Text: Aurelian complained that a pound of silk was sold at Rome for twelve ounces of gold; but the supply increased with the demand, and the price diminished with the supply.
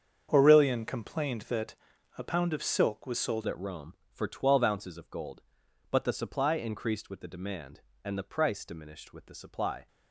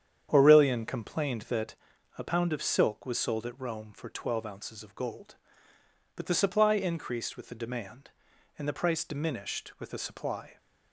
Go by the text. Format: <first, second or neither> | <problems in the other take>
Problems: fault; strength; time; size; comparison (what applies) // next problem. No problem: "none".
second | starts louder than the rest; strong; until 1.3 s; 7 dB; strong in the second // pauses between "that" and "a"; at 1.7 s; 0.42 s long; also in the second // changes voice at "at"; from 3.4 s on; 6.4 s long